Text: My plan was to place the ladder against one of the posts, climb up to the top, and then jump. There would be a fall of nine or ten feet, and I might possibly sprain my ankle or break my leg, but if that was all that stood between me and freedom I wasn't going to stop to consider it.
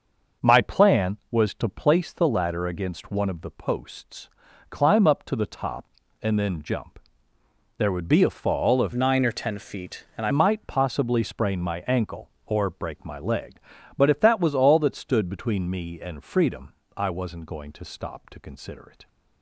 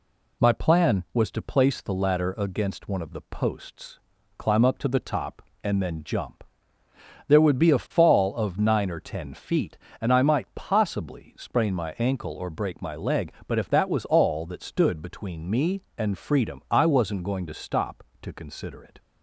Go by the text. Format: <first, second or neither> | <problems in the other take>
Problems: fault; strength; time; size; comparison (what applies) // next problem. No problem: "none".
second | starts louder than the rest; noticeable; until 1.5 s; 6 dB // changes voice from "nine" to "I"; from 8.9 to 10.3 s; 1.4 s long // pauses between "freedom" and "I"; slight; at 16.7 s; 0.24 s long